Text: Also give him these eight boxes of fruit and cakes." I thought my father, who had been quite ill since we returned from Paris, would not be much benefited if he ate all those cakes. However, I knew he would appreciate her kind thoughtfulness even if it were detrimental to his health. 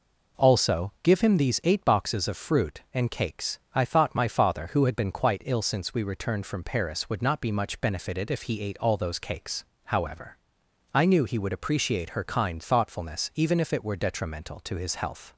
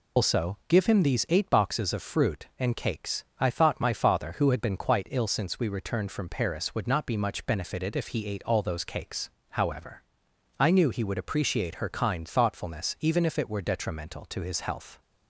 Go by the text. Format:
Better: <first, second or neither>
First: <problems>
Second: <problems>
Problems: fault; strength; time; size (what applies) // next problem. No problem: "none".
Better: first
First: none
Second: loses the start of "Also"; at 0.1 s; 145 ms